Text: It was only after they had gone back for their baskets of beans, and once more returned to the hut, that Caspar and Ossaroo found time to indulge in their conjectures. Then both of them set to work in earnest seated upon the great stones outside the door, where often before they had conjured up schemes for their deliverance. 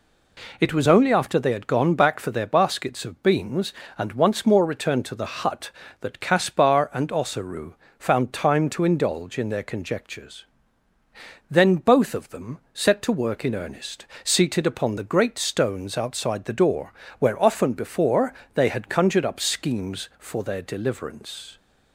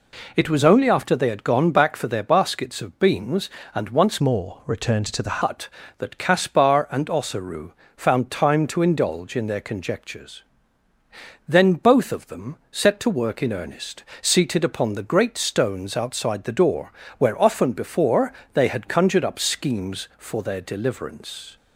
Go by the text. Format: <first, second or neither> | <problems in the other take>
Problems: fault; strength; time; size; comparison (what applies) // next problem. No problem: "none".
first | changes voice from "more" to "the"; from 4.2 to 5.4 s; 1.2 s long // pauses between "Ossaroo" and "found"; slight; at 7.7 s; 0.26 s long; slight in the first // pauses between "earnest" and "seated"; slight; at 14.0 s; 0.18 s long; slight in the first // pauses between "before" and "they"; slight; at 18.3 s; 0.20 s long; slight in the first